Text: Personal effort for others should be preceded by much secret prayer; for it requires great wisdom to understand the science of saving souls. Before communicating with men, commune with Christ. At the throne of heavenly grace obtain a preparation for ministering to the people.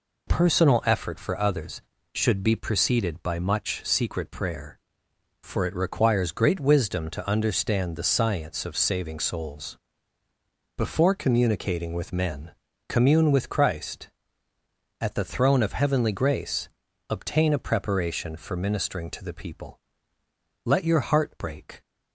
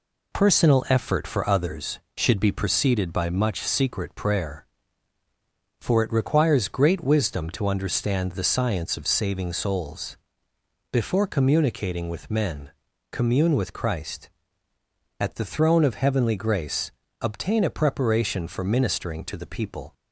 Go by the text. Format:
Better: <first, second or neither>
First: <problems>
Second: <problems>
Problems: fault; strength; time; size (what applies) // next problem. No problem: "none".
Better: second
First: pauses between "grace" and "obtain"; at 16.6 s; 0.40 s long // goes on to say "Let your heart break"; noticeable; from 20.6 s on; 1.1 s long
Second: pauses between "grace" and "obtain"; slight; at 16.9 s; 0.30 s long